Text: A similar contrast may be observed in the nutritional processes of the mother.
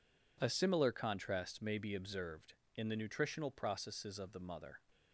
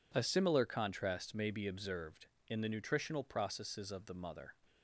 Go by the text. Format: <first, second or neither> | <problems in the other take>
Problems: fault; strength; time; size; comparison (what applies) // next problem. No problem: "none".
neither | none